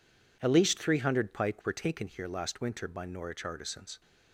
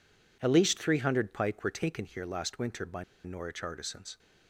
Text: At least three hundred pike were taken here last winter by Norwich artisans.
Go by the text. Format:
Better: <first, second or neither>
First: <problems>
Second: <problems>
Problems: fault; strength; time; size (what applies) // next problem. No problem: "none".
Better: first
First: none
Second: pauses between "by" and "Norwich"; slight; at 3.0 s; 0.22 s long